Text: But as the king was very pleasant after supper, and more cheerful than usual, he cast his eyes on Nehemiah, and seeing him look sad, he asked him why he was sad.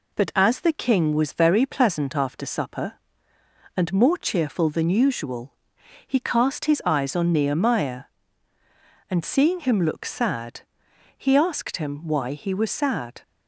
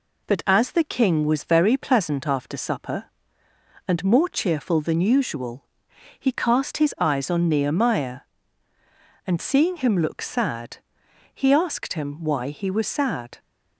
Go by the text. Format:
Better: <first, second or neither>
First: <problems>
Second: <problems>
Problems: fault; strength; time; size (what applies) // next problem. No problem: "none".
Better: neither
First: none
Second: none